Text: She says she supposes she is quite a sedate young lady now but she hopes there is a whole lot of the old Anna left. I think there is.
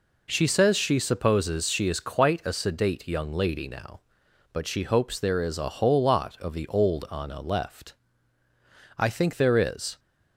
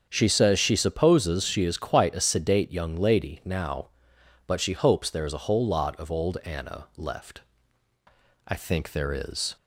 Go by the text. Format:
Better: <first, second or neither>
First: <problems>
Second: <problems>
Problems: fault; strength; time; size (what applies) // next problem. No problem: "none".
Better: first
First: none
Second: starts louder than the rest; until 1.1 s; 7 dB // skips "the"; at 6.0 s